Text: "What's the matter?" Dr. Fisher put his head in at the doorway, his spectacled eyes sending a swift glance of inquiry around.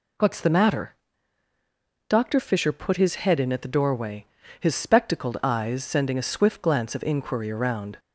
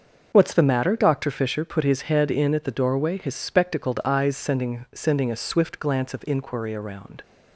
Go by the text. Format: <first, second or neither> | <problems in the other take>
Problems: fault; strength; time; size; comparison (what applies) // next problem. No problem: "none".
first | starts louder than the rest; until 1.3 s; 6.5 dB // says "sending" twice; at 4.9 s